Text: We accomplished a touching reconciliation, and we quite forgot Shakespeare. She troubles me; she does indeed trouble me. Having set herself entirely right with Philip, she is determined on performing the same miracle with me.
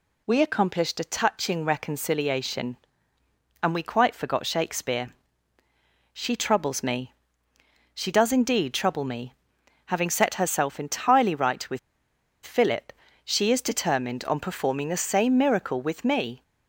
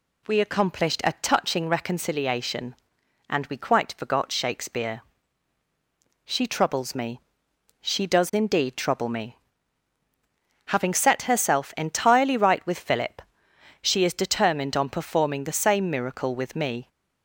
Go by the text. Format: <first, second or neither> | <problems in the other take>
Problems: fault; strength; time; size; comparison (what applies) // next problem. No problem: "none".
second | pauses between "with" and "Philip"; noticeable; at 11.7 s; 0.65 s long